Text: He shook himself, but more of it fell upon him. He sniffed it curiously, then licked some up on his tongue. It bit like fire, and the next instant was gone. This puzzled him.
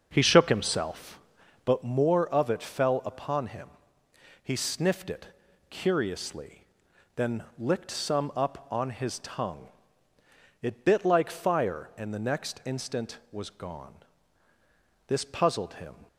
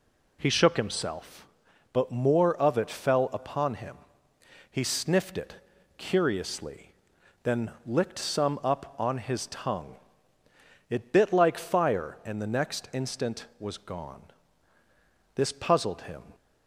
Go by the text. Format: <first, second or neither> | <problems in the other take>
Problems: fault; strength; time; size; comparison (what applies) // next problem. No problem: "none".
second | starts louder than the rest; until 1.8 s; 6.5 dB // pauses between "it" and "curiously"; at 5.2 s; 0.42 s long; also in the second